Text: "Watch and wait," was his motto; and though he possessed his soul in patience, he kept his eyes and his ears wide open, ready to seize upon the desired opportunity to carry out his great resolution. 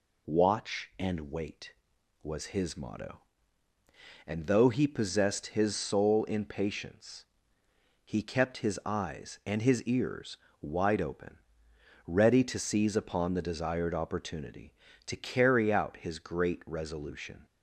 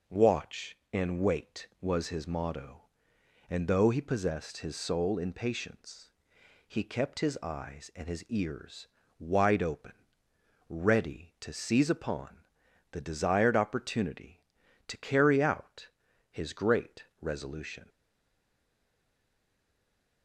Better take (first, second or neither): first